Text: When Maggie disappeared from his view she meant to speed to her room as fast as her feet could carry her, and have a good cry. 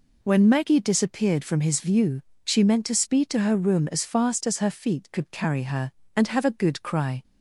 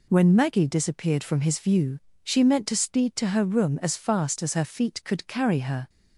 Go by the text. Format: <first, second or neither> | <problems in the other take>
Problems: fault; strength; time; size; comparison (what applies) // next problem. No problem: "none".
first | pauses between "view" and "she"; slight; at 1.9 s; 0.24 s long; slight in the first // stops before "and have a good cry"; at 5.8 s